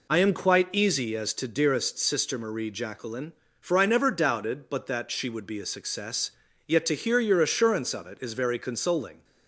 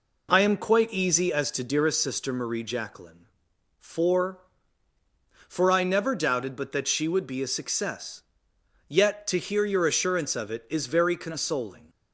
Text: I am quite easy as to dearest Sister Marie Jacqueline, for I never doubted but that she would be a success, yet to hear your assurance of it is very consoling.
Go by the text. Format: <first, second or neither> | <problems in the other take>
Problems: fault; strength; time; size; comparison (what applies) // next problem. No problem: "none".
first | says "for" twice; at 5.4 s